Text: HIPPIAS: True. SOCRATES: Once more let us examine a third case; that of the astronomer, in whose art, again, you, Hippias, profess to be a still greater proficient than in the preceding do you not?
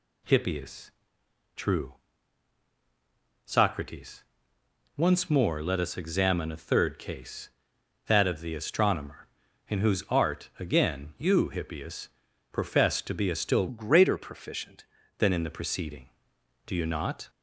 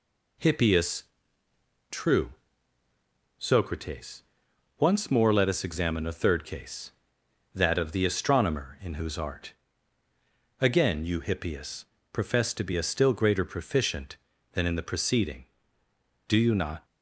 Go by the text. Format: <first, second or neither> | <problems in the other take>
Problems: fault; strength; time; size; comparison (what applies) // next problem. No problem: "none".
second | changes voice from "greater" to "proficient"; from 13.6 to 14.8 s; 1.2 s long